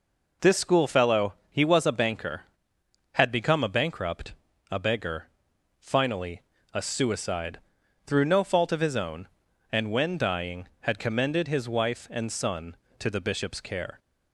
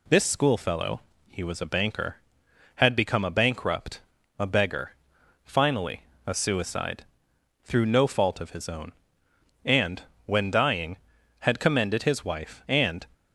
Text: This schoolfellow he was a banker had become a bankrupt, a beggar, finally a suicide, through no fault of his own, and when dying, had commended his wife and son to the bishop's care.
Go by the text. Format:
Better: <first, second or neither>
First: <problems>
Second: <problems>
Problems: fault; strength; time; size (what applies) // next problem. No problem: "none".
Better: first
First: pauses between "schoolfellow" and "he"; slight; at 1.3 s; 0.16 s long // pauses between "finally" and "a"; slight; at 6.4 s; 0.28 s long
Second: pauses between "schoolfellow" and "he"; slight; at 1.0 s; 0.28 s long // pauses between "finally" and "a"; slight; at 6.0 s; 0.24 s long // pauses between "and" and "when"; slight; at 10.0 s; 0.24 s long // stops before "son to the bishop's care"; at 13.1 s